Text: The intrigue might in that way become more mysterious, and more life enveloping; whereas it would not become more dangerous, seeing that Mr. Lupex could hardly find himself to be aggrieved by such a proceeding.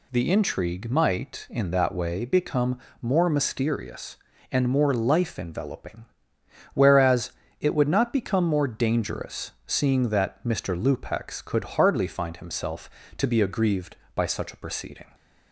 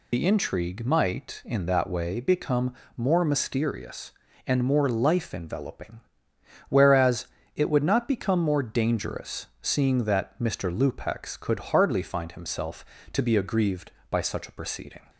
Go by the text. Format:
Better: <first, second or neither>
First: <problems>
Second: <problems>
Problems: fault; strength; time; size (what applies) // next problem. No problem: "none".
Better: first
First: pauses between "become" and "more"; slight; at 2.7 s; 0.22 s long // pauses between "whereas" and "it"; slight; at 7.3 s; 0.30 s long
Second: loses the start of "The"; at 0.1 s; 70 ms // pauses between "become" and "more"; slight; at 2.7 s; 0.22 s long // pauses between "whereas" and "it"; slight; at 7.2 s; 0.30 s long